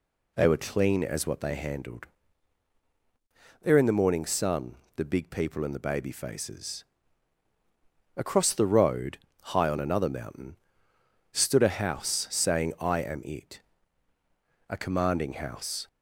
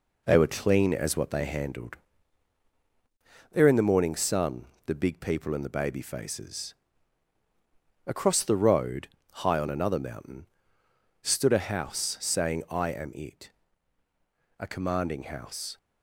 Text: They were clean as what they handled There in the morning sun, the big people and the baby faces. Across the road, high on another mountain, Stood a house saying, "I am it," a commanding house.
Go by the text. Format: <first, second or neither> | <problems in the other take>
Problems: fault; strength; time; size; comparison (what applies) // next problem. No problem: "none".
first | gets quieter; noticeable; throughout; 4.5 dB // pauses between "handled" and "There"; strong; at 1.9 s; 1.5 s long; strong in the first